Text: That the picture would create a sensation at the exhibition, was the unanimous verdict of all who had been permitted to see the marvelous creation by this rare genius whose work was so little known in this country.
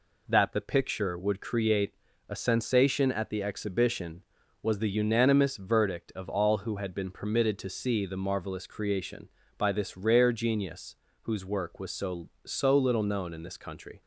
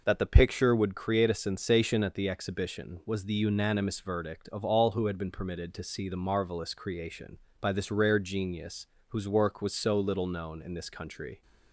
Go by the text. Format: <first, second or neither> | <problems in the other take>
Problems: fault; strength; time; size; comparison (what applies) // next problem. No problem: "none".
second | pauses between "create" and "a"; slight; at 1.9 s; 0.34 s long // pauses between "genius" and "whose"; slight; at 10.9 s; 0.26 s long; slight in the second // says "so" twice; at 12.4 s